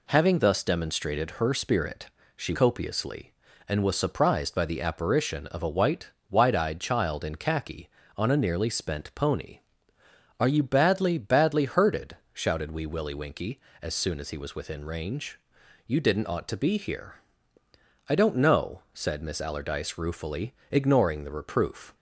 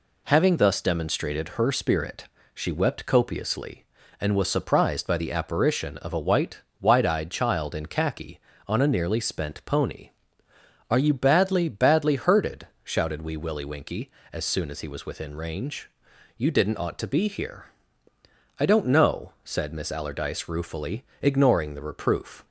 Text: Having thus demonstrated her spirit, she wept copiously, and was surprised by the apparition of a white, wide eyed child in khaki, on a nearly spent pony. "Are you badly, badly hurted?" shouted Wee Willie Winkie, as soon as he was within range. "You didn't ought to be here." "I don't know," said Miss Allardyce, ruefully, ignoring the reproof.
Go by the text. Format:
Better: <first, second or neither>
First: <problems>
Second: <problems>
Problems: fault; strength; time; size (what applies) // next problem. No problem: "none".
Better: second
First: skips "wept"; at 2.5 s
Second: none